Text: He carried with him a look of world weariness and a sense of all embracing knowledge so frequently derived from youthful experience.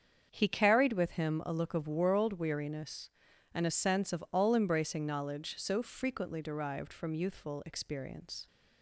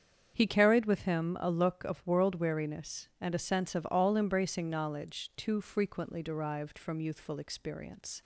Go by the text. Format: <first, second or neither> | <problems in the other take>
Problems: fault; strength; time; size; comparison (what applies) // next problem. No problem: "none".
first | starts louder than the rest; strong; until 1.3 s; 7.5 dB; strong in the first // says "too" for "so"; at 5.3 s